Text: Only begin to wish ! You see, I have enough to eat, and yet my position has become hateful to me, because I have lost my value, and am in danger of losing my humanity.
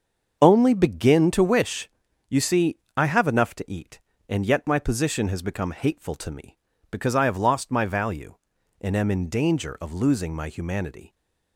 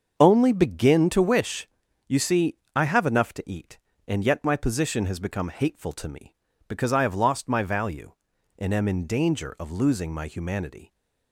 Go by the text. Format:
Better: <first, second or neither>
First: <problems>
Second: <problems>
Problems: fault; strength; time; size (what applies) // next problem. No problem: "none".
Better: neither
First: starts louder than the rest; until 1.4 s; 6.5 dB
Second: starts louder than the rest; until 1.1 s; 6.5 dB